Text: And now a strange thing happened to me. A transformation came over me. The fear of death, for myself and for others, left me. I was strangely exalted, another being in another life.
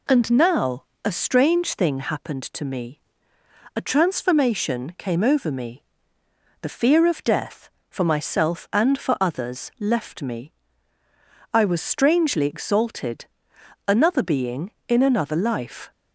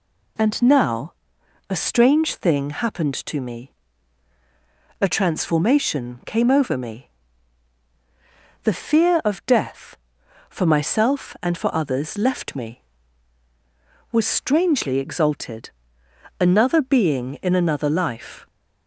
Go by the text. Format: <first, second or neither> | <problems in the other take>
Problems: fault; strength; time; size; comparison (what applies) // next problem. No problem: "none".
first | pauses between "now" and "a"; noticeable; at 1.1 s; 0.54 s long; slight in the first // skips "I"; at 13.4 s